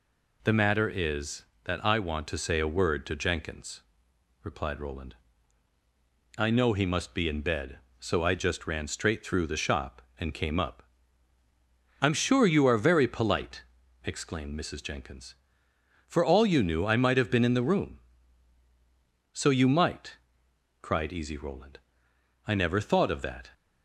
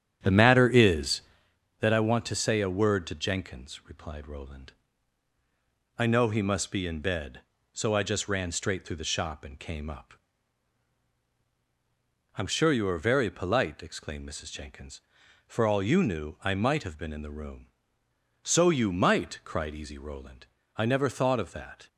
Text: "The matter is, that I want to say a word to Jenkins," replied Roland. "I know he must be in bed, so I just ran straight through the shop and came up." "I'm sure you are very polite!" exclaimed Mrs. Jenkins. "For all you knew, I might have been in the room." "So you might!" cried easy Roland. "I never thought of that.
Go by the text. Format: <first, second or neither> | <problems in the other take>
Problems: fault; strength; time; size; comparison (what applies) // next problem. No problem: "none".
first | starts louder than the rest; strong; until 1.6 s; 9.5 dB